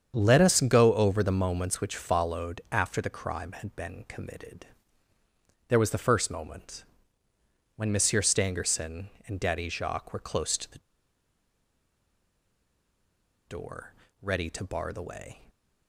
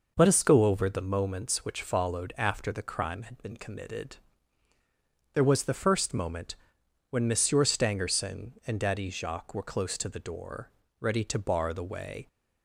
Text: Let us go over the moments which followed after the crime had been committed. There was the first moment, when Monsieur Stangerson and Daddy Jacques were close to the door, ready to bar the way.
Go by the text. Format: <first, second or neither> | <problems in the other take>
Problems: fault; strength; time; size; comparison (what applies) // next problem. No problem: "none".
second | starts louder than the rest; strong; until 1.1 s; 8 dB // pauses between "the" and "door"; strong; at 10.7 s; 2.6 s long